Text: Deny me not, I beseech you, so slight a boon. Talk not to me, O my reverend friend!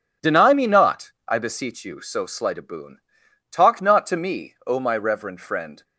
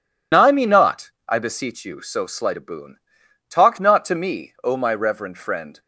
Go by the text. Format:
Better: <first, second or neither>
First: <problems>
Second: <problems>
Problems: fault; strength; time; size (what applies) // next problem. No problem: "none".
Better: first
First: none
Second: loses the start of "Deny"; at 0.3 s; 120 ms